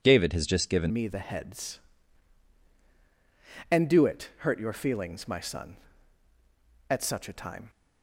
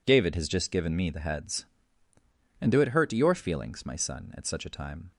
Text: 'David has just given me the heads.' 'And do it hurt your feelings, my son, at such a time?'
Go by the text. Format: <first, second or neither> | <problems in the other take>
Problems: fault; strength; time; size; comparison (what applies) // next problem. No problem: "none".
second | changes voice at "me"; from 0.9 s on; 6.7 s long